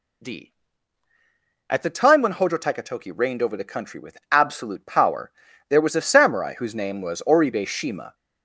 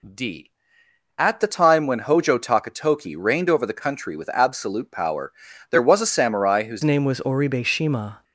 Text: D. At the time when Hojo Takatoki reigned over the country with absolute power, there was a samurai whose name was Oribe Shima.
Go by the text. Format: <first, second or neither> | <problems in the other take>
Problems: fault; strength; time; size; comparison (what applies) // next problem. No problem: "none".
first | changes voice at "name"; from 6.8 s on; 1.4 s long